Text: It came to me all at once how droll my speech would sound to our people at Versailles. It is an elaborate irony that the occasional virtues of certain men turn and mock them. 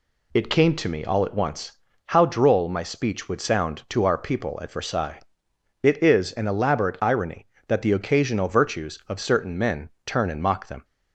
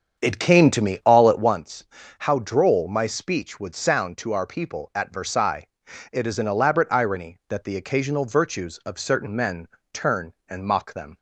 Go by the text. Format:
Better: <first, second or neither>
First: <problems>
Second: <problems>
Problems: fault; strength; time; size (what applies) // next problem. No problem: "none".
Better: first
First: pauses between "once" and "how"; slight; at 1.7 s; 0.34 s long // pauses between "men" and "turn"; slight; at 9.9 s; 0.16 s long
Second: starts louder than the rest; strong; until 1.6 s; 7.5 dB // pauses between "once" and "how"; slight; at 1.8 s; 0.34 s long // pauses between "men" and "turn"; slight; at 9.6 s; 0.26 s long